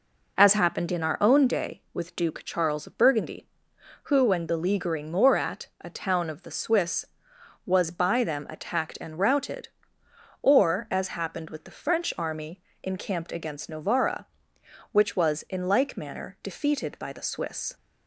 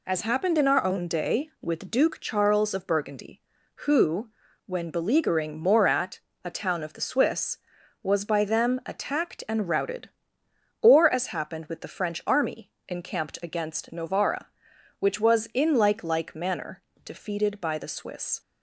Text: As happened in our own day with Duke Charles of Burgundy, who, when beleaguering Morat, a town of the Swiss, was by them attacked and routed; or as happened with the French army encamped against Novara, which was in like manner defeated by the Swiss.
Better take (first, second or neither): first